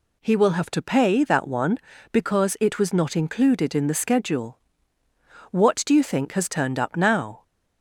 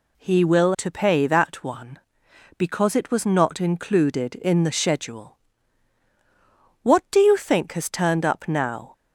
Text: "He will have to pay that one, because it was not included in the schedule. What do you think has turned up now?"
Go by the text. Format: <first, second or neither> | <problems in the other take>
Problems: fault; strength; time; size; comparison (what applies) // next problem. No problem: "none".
first | skips "have"; at 0.7 s